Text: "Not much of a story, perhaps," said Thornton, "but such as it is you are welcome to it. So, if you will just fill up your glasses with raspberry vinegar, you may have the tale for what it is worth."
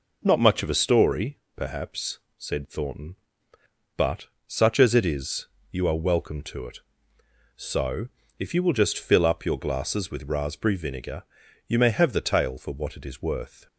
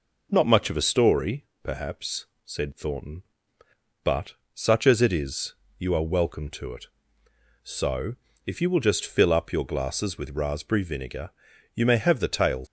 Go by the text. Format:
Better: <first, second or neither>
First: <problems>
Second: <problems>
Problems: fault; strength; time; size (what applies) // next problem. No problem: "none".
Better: first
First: pauses between "but" and "such"; slight; at 4.2 s; 0.20 s long // pauses between "is" and "you"; slight; at 5.4 s; 0.26 s long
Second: pauses between "but" and "such"; slight; at 4.3 s; 0.20 s long // pauses between "is" and "you"; slight; at 5.5 s; 0.26 s long // stops before "for what it is worth"; at 12.6 s